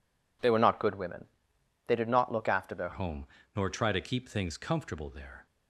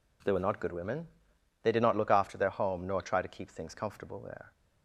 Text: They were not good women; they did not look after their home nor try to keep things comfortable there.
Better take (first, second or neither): second